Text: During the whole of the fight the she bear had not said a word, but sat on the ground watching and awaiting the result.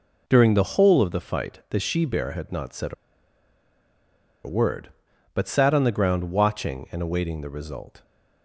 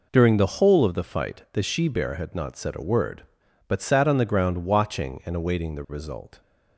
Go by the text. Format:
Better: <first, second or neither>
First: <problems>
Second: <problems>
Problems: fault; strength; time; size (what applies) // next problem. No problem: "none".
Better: second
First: pauses between "a" and "word"; strong; at 2.9 s; 1.5 s long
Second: none